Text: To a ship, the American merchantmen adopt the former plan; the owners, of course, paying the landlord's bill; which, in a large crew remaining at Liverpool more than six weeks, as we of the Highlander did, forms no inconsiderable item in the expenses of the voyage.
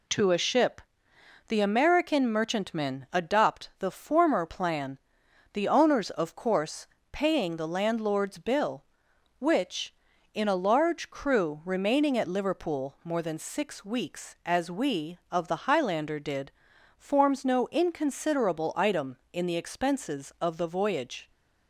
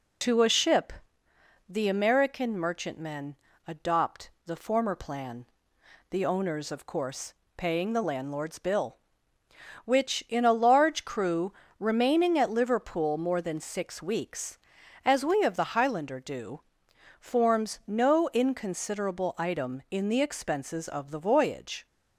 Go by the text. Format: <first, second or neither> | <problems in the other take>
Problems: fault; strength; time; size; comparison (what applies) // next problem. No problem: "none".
first | pauses between "merchantmen" and "adopt"; slight; at 3.3 s; 0.32 s long // pauses between "adopt" and "the"; slight; at 4.3 s; 0.16 s long // pauses between "crew" and "remaining"; slight; at 11.5 s; 0.24 s long // says "do" for "did"; at 16.2 s